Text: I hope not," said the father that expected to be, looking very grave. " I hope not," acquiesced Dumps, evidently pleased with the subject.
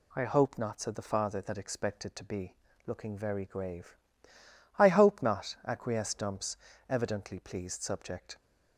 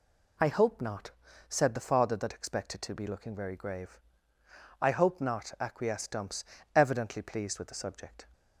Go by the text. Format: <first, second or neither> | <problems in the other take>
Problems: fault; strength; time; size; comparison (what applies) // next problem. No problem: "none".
second | skips "with the"; at 7.8 s